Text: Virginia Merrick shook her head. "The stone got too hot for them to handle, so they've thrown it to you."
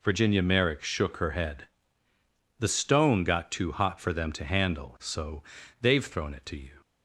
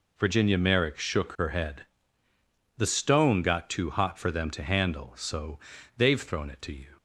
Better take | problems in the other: neither | pauses between "so" and "they've"; slight; the same in both

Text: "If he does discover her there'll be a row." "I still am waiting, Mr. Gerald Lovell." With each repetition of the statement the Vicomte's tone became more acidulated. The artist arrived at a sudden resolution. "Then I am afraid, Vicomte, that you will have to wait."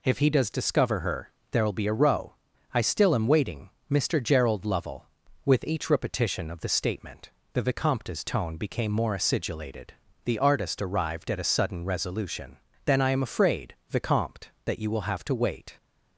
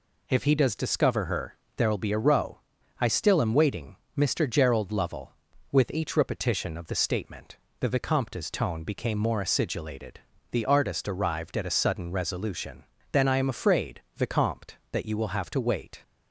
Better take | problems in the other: neither | pauses between "her" and "there'll"; slight; the same in both // pauses between "statement" and "the"; slight; the same in both

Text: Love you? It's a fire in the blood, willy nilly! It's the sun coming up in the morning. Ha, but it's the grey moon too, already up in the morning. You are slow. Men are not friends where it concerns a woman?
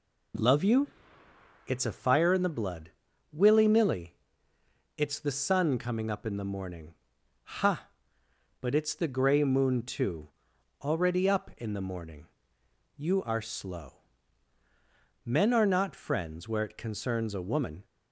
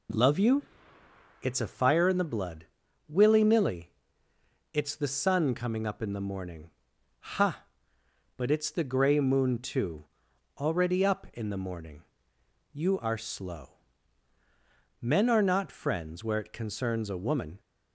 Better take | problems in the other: neither | none

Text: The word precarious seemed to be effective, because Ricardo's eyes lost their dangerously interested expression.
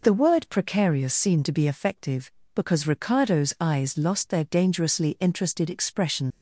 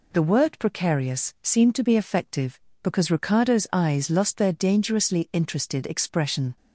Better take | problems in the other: second | leaves "expression" unfinished; at 6.3 s; 80 ms

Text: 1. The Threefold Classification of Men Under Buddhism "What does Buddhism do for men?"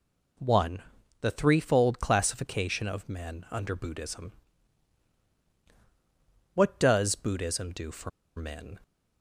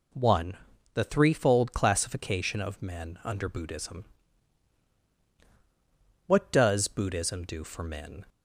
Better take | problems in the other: second | pauses between "Buddhism" and "What"; strong; at 4.3 s; 2.2 s long; strong in the second // pauses between "for" and "men"; slight; at 8.0 s; 0.27 s long

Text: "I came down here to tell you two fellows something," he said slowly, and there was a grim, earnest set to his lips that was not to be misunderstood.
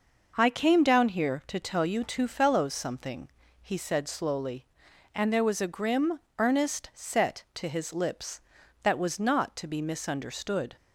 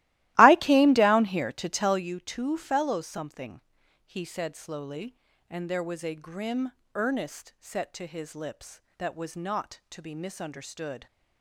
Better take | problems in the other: first | starts louder than the rest; strong; until 2.1 s; 17 dB

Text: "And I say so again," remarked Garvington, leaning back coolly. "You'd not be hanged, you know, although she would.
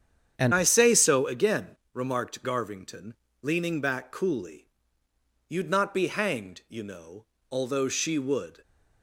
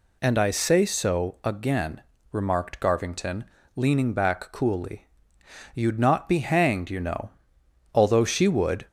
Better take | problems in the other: second | starts louder than the rest; strong; until 1.3 s; 8.5 dB // changes voice at "I"; from 0.5 s on; 8.1 s long

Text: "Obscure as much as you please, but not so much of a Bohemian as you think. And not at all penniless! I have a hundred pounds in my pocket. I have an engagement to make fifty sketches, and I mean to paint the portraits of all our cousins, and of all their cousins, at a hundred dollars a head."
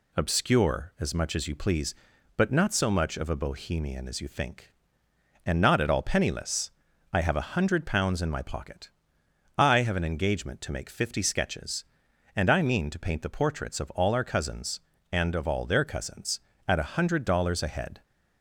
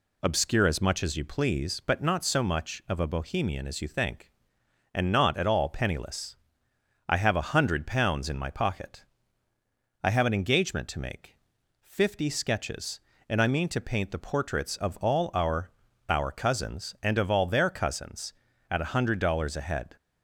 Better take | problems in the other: first | pauses between "make" and "fifty"; at 11.3 s; 0.44 s long // says "our" twice; at 16.0 s

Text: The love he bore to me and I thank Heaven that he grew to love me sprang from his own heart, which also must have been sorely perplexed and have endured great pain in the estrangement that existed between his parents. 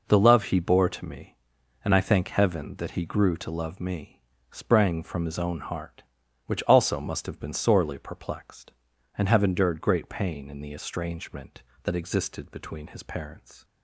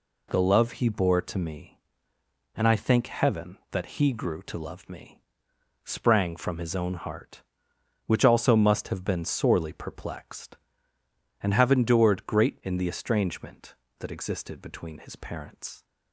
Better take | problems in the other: first | pauses between "me" and "sprang"; noticeable; at 5.2 s; 0.64 s long; slight in the first // skips "pain"; at 12.6 s

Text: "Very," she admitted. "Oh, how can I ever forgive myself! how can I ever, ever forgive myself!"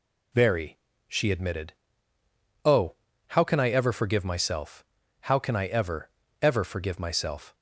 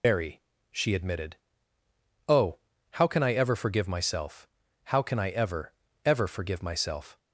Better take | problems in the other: first | loses the start of "Very"; at 0.0 s; 75 ms

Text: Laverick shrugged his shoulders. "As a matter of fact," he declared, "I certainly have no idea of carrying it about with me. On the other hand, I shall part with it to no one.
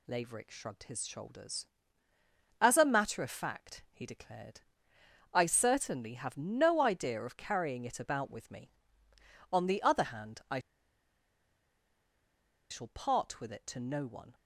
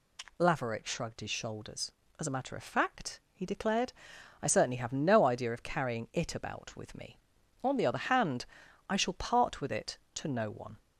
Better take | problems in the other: second | pauses between "I" and "shall"; strong; at 10.5 s; 2.1 s long

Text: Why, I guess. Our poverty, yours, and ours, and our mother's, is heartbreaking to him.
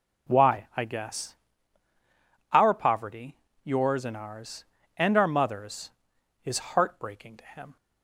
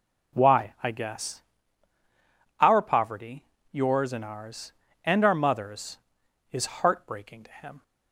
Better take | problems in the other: neither | none

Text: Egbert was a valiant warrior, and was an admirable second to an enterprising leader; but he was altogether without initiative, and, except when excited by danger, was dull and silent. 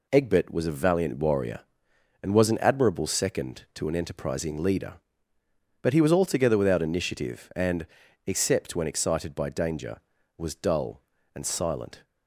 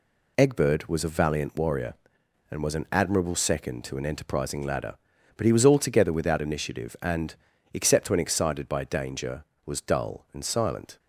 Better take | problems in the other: first | says "ladder" for "leader"; at 4.6 s

